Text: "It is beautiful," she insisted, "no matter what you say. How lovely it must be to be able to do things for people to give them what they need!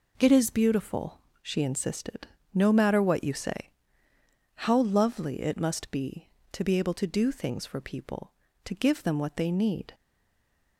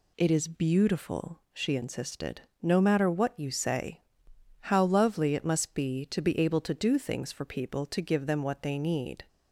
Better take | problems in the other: second | stays silent after the last word; slight; from 9.9 s on; 0.8 s long

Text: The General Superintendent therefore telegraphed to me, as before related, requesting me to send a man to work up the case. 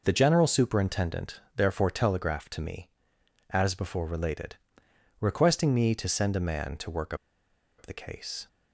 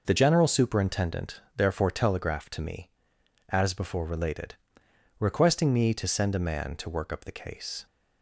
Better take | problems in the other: second | pauses between "Superintendent" and "therefore"; slight; at 1.4 s; 0.16 s long; slight in the second // pauses between "work" and "up"; noticeable; at 7.1 s; 0.63 s long

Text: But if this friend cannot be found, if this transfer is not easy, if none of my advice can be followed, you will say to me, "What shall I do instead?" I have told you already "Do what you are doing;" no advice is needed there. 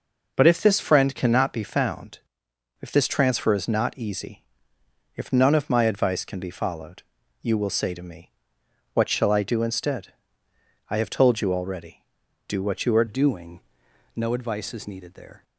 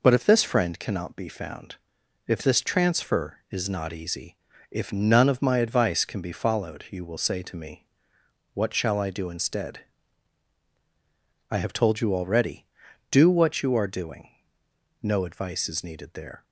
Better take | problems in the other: second | changes voice at "doing"; from 13.0 s on; 2.4 s long

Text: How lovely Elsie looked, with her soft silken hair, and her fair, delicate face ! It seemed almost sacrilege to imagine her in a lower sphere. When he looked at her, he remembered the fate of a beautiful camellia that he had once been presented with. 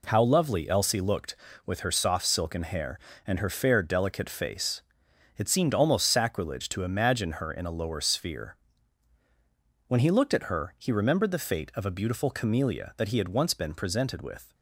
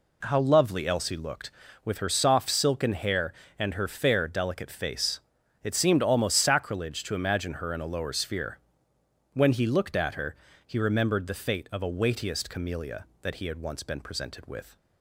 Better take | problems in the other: first | says "weightiest" for "beautiful"; at 11.8 s

